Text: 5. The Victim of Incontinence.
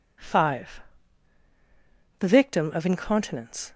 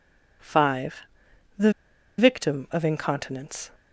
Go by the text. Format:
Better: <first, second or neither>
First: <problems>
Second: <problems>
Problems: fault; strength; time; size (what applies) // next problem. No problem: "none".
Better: first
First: none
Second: pauses between "The" and "Victim"; noticeable; at 1.6 s; 0.48 s long